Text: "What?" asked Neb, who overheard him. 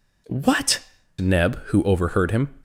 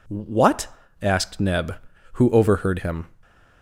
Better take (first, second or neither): second